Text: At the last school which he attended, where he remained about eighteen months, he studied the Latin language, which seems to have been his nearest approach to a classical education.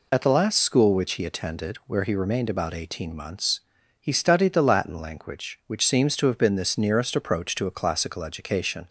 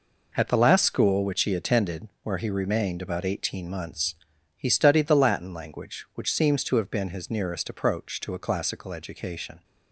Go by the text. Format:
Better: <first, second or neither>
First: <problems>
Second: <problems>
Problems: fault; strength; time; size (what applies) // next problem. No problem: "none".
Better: second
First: says "this" for "his"; at 6.5 s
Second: none